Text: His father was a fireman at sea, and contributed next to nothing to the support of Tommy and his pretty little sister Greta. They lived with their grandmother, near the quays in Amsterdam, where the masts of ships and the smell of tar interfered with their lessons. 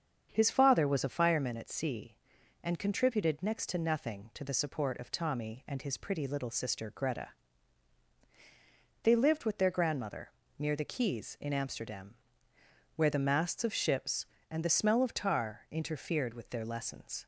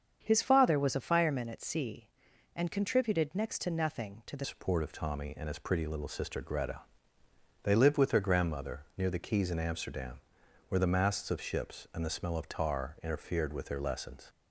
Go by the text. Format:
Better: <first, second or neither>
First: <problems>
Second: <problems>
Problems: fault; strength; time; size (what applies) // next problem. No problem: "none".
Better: first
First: starts louder than the rest; strong; until 1.3 s; 7 dB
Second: starts louder than the rest; strong; until 1.2 s; 7.5 dB // changes voice at "support"; from 4.4 s on; 9.8 s long